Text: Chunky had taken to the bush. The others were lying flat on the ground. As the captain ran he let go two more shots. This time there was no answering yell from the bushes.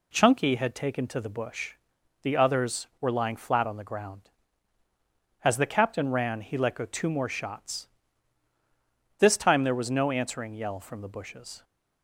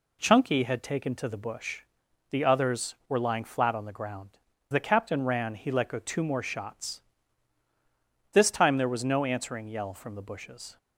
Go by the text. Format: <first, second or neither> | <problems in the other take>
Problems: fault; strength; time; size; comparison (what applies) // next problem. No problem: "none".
first | skips "As"; at 4.5 s